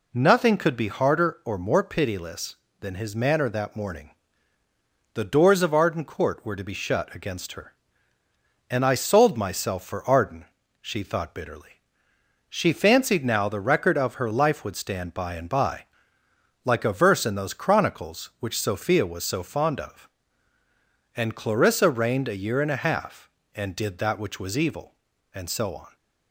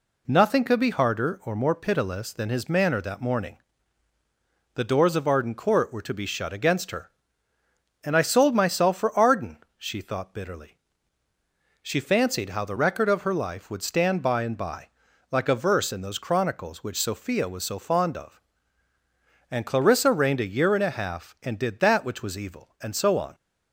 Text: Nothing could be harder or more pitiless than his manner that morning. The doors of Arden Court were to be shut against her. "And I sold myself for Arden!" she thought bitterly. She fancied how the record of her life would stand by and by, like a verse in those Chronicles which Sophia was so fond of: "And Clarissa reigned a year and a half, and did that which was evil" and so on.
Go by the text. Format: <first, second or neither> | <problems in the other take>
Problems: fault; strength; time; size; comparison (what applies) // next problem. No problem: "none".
second | says "now" for "how"; at 13.2 s